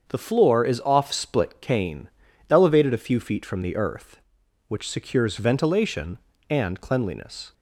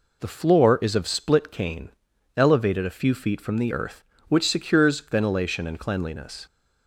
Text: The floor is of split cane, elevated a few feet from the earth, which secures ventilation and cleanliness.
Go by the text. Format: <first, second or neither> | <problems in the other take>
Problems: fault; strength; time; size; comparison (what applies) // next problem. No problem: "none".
second | starts louder than the rest; until 1.0 s; 7 dB // says "off" for "of"; at 0.8 s